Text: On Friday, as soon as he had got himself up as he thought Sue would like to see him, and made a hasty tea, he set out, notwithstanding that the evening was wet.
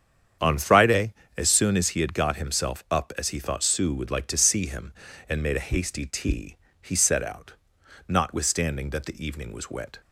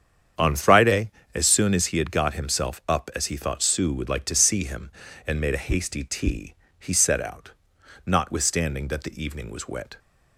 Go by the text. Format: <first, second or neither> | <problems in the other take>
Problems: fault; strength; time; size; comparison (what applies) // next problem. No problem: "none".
neither | starts louder than the rest; strong; the same in both